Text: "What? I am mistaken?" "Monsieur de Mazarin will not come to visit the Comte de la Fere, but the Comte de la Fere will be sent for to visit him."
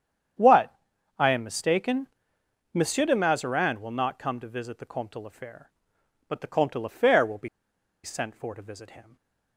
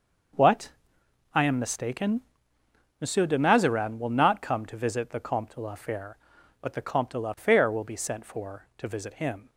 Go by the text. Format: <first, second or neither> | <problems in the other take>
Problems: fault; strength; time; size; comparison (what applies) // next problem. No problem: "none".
second | starts louder than the rest; strong; until 1.7 s; 8.5 dB; also in the second // pauses between "be" and "sent"; noticeable; at 7.4 s; 0.55 s long // stays silent after the last word; slight; from 9.0 s on; 0.5 s long